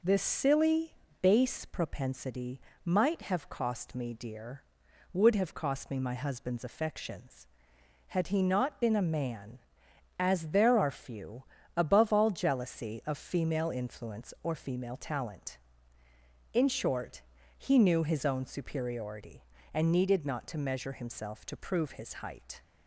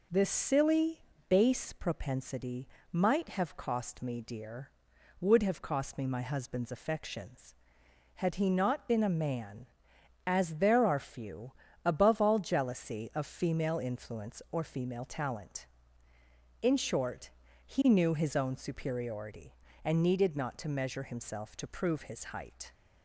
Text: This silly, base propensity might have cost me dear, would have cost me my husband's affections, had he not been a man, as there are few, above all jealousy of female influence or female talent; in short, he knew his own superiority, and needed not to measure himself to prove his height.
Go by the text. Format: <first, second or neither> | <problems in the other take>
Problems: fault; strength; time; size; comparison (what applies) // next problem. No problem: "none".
neither | pauses between "propensity" and "might"; slight; the same in both